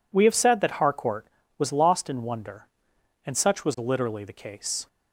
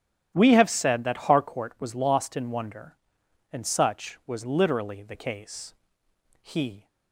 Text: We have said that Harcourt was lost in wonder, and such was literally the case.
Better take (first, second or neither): first